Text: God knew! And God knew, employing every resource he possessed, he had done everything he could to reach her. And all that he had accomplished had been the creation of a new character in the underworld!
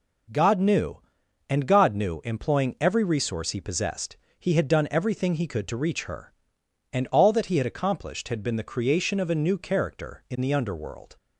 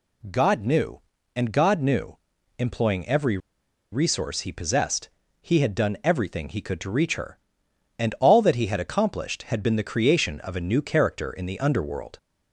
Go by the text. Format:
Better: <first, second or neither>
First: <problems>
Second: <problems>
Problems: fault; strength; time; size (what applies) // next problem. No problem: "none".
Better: first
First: none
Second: pauses between "every" and "resource"; noticeable; at 3.3 s; 0.54 s long